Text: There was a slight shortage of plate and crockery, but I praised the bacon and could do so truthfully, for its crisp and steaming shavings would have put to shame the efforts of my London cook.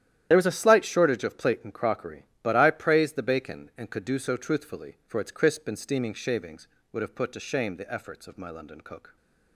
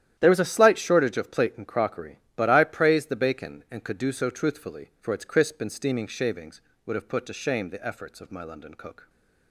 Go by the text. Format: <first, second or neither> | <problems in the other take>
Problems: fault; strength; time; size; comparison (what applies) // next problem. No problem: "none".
second | loses the start of "There"; at 0.3 s; 50 ms // starts louder than the rest; strong; until 1.3 s; 11.5 dB; strong in the second